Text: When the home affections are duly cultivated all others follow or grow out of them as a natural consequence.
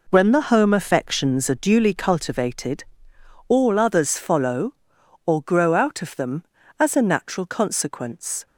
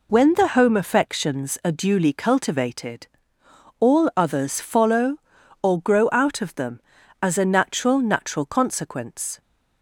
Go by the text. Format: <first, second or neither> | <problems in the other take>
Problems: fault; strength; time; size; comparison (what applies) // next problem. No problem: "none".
first | pauses between "cultivated" and "all"; noticeable; at 3.0 s; 0.72 s long; noticeable in the first // says "natural" twice; at 8.0 s